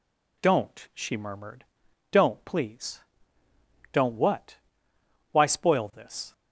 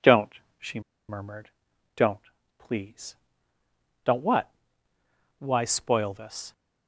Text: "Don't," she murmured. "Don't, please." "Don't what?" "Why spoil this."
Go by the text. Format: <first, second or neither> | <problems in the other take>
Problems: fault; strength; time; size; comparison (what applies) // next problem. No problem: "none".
first | pauses between "she" and "murmured"; slight; at 0.8 s; 0.28 s long